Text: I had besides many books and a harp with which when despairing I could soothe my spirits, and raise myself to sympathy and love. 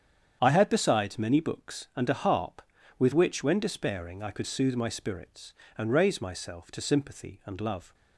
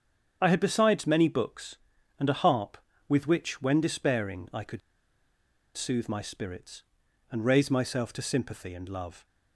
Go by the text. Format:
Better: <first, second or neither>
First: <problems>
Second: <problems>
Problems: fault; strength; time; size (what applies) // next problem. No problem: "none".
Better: first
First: starts louder than the rest; strong; until 1.4 s; 8.5 dB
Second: starts louder than the rest; strong; until 1.4 s; 8 dB // pauses between "could" and "soothe"; noticeable; at 4.8 s; 0.95 s long